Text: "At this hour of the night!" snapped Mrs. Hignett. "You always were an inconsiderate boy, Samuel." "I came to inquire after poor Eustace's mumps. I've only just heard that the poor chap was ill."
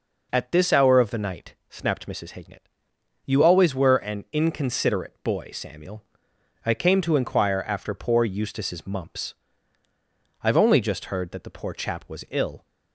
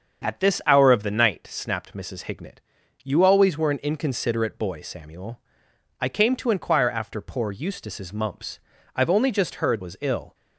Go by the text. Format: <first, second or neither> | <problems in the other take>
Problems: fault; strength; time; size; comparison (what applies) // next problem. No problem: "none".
first | starts louder than the rest; strong; until 1.2 s; 7.5 dB // skips "that the poor chap"; at 9.8 s